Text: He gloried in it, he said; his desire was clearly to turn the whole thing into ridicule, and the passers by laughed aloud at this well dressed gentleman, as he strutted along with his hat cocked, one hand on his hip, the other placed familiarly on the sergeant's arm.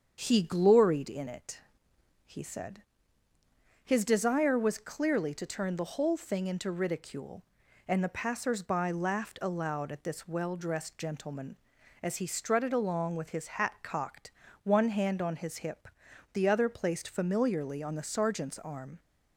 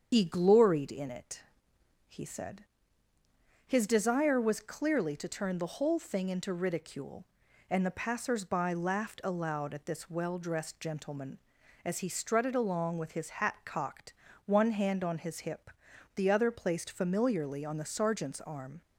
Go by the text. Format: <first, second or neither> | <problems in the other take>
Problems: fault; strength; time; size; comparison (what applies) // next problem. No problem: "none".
first | loses the start of "He"; at 0.1 s; 120 ms // starts louder than the rest; strong; until 1.1 s; 7.5 dB; strong in the first